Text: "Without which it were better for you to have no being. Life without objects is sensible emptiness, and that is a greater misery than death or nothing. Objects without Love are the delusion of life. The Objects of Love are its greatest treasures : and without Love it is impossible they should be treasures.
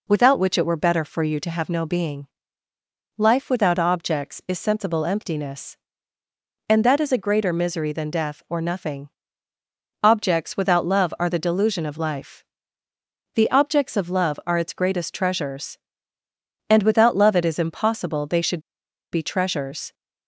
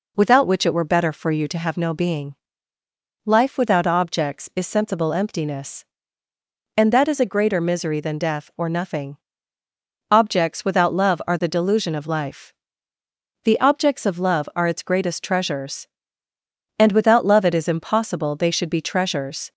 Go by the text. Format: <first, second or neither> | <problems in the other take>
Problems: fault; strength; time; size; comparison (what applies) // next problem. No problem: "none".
second | pauses between "should" and "be"; noticeable; at 18.6 s; 0.51 s long